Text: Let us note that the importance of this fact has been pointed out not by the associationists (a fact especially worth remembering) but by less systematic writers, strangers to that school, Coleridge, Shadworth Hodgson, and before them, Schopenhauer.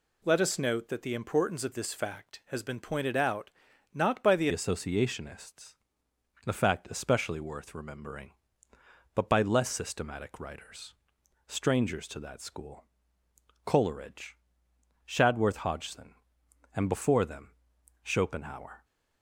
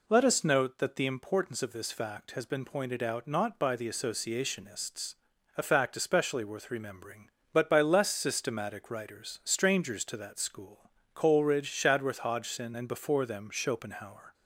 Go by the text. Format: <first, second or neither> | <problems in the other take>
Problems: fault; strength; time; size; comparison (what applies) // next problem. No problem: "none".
second | pauses between "out" and "not"; at 3.5 s; 0.42 s long // changes voice at "associationists"; from 4.5 s on; 14.3 s long